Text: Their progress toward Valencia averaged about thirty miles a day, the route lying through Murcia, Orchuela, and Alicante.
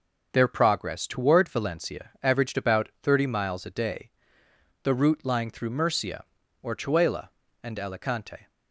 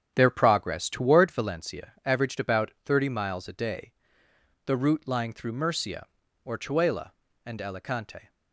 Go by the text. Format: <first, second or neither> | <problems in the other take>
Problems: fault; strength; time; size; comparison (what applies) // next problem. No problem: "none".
first | starts louder than the rest; strong; until 1.5 s; 9 dB